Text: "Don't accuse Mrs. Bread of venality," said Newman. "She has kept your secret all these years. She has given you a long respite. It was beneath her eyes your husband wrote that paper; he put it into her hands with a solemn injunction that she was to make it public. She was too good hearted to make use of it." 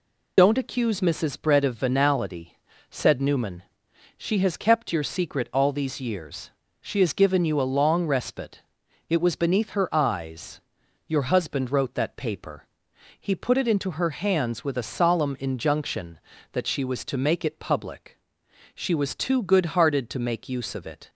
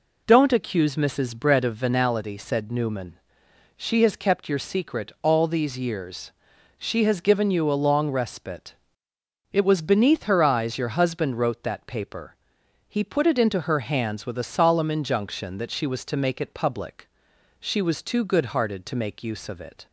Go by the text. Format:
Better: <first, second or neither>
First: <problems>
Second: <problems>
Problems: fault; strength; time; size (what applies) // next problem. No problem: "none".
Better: second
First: loses the start of "Don't"; at 0.3 s; 45 ms // pauses between "eyes" and "your"; noticeable; at 10.6 s; 0.46 s long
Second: none